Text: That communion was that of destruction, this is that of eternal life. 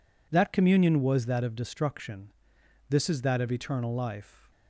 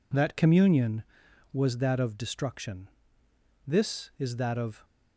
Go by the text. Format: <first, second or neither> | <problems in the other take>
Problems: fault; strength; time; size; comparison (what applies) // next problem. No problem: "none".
first | stops before "eternal life"; at 4.8 s